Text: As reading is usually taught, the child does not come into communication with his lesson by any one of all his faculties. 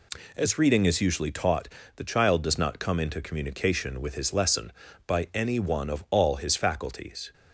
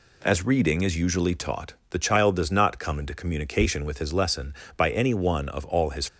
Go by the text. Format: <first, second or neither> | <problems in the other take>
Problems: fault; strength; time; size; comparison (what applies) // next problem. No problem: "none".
first | stops before "faculties"; at 6.0 s